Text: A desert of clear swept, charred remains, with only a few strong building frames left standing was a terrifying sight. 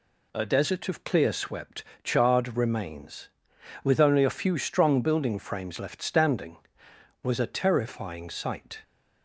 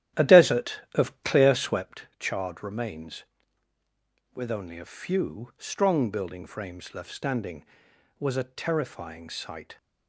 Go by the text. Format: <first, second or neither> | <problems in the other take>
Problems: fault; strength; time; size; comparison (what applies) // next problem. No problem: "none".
first | starts louder than the rest; strong; until 1.8 s; 11.5 dB